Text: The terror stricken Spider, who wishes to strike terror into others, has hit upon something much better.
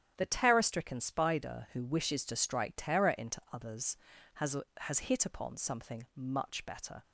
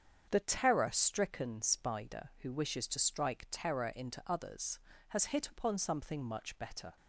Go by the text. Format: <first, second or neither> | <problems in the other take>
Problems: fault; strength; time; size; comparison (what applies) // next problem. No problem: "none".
second | starts louder than the rest; strong; until 1.1 s; 10 dB; strong in the second // says "has" twice; at 4.7 s